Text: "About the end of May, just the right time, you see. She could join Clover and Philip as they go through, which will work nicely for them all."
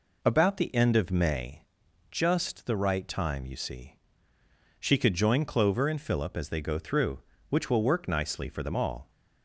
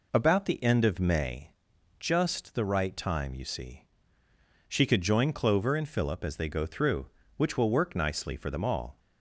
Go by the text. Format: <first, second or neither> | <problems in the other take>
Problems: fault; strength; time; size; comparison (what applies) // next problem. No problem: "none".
neither | none